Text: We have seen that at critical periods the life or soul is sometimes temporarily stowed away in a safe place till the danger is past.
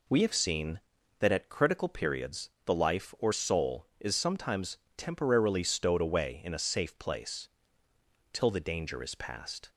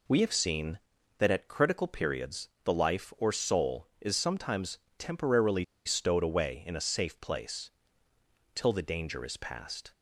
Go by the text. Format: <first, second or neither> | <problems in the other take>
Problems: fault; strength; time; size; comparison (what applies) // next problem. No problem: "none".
first | pauses between "periods" and "the"; slight; at 2.4 s; 0.16 s long; slight in the first // pauses between "sometimes" and "temporarily"; slight; at 4.7 s; 0.22 s long; slight in the first // pauses between "temporarily" and "stowed"; slight; at 5.6 s; 0.21 s long // pauses between "place" and "till"; noticeable; at 7.7 s; 0.84 s long; noticeable in the first